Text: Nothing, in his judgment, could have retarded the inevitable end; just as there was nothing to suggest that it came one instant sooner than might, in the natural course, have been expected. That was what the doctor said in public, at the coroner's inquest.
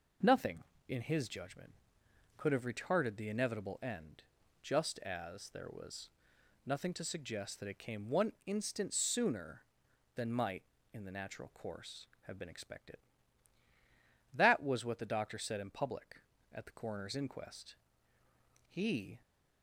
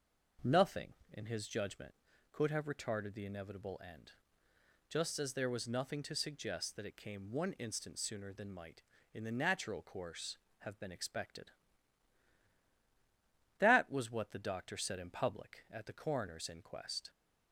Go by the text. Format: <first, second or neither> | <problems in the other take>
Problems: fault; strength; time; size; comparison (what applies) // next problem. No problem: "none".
second | pauses between "was" and "nothing"; noticeable; at 6.0 s; 0.54 s long // goes on to say "He"; from 18.6 s on; 0.54 s long